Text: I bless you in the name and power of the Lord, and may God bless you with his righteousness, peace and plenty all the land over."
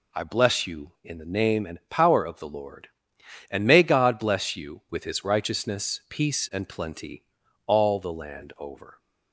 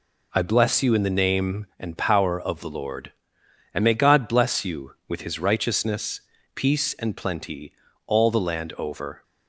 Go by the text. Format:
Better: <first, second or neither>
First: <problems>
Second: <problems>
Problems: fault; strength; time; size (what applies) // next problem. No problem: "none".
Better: neither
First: pauses between "plenty" and "all"; at 7.2 s; 0.40 s long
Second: pauses between "plenty" and "all"; slight; at 7.7 s; 0.36 s long